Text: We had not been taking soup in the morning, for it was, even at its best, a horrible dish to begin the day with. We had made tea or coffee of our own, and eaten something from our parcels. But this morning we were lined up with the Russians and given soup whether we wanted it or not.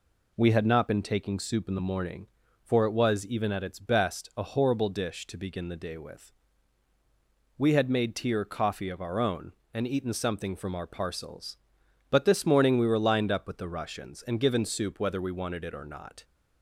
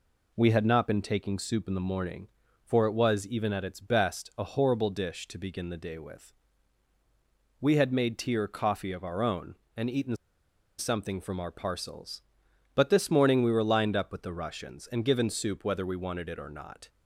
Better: first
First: none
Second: pauses between "eaten" and "something"; noticeable; at 10.1 s; 0.62 s long

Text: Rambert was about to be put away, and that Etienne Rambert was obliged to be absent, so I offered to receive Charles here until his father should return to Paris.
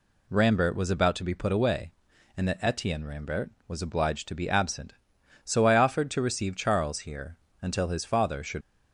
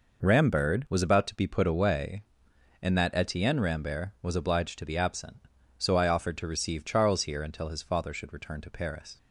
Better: second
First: pauses between "here" and "until"; slight; at 7.3 s; 0.24 s long // stops before "return to Paris"; at 8.6 s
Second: none

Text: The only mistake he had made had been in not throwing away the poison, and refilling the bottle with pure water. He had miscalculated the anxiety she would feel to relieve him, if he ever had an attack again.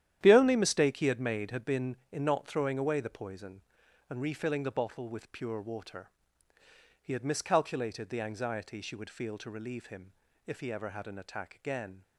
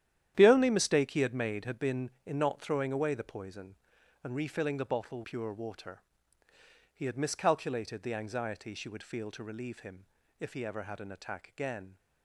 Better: first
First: starts louder than the rest; strong; until 1.2 s; 10.5 dB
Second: starts louder than the rest; strong; until 1.3 s; 10.5 dB // skips "with"; at 5.2 s

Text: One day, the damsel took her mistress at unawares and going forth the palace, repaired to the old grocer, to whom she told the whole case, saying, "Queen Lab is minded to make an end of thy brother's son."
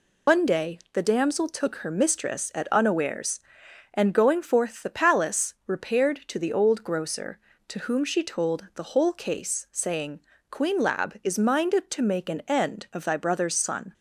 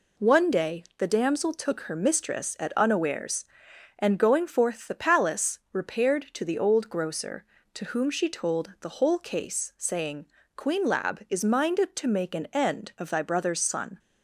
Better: second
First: loses the start of "One"; at 0.2 s; 140 ms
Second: none

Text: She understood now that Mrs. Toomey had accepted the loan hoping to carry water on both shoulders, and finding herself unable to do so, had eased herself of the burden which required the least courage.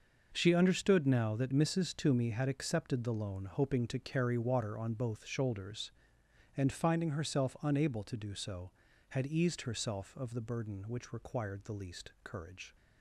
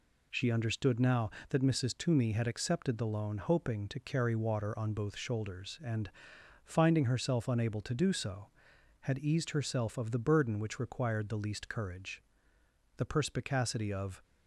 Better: first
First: none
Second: pauses between "and" and "finding"; noticeable; at 6.0 s; 0.56 s long // goes on to say "The perspicacity of"; noticeable; from 12.9 s on; 1.2 s long

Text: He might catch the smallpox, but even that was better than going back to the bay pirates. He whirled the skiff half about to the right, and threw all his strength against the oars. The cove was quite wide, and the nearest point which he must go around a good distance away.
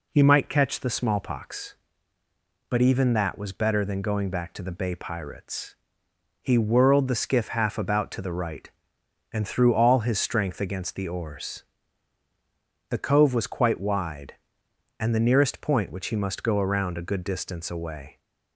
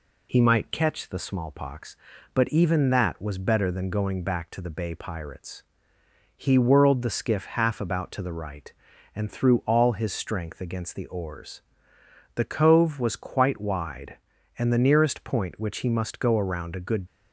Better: first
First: none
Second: stops before "distance away"; at 17.0 s

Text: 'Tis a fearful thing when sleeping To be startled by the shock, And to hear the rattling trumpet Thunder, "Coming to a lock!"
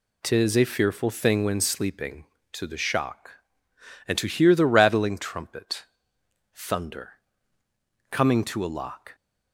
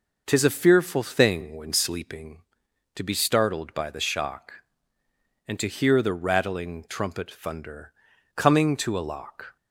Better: second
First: skips "be startled by"; at 2.6 s // pauses between "trumpet" and "Thunder"; noticeable; at 5.8 s; 0.66 s long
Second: none

